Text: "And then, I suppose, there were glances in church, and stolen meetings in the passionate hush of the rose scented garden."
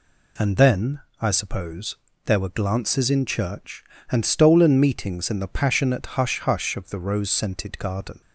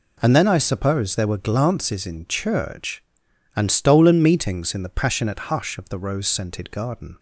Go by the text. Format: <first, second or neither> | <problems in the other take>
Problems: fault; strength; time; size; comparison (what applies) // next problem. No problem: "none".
second | says "hush" twice; at 6.4 s